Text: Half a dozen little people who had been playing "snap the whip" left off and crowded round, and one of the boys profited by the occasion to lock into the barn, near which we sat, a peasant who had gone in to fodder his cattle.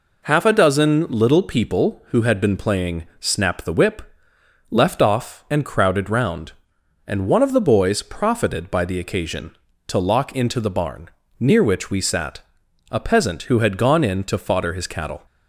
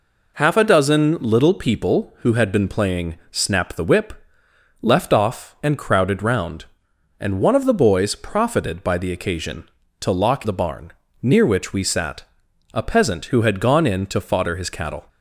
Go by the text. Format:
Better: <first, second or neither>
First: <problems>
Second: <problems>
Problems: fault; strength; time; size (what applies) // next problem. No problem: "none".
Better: first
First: pauses between "whip" and "left"; noticeable; at 4.0 s; 0.70 s long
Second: pauses between "whip" and "left"; noticeable; at 4.1 s; 0.70 s long // skips "into"; at 10.4 s